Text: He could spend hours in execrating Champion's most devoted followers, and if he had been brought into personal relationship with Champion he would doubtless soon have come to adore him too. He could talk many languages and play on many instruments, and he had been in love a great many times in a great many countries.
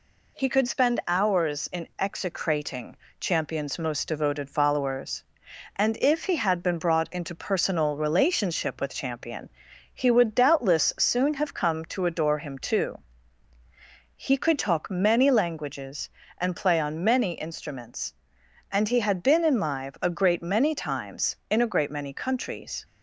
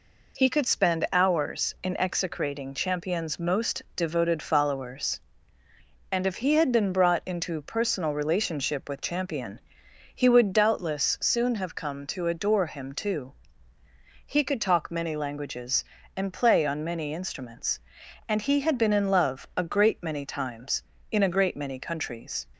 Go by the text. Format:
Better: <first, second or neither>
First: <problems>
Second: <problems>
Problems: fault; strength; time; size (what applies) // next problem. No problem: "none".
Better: second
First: pauses between "execrating" and "Champion's"; slight; at 2.9 s; 0.24 s long // pauses between "Champion" and "he"; at 9.4 s; 0.44 s long // says "live" for "love"; at 19.6 s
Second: pauses between "Champion" and "he"; noticeable; at 9.5 s; 0.54 s long